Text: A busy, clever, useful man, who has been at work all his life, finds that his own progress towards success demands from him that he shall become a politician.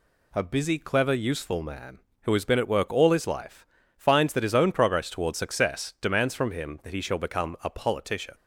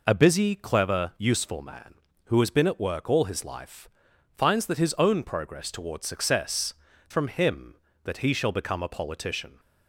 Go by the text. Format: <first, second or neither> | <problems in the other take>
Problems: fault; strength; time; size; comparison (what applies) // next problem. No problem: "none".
first | skips "demands"; at 6.9 s